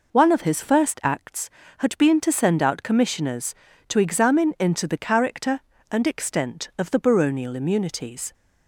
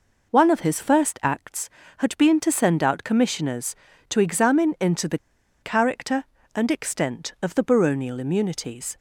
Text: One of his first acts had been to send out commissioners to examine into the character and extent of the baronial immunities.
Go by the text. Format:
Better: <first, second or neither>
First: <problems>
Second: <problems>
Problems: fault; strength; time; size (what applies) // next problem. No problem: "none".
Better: first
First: none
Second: pauses between "the" and "character"; at 5.1 s; 0.45 s long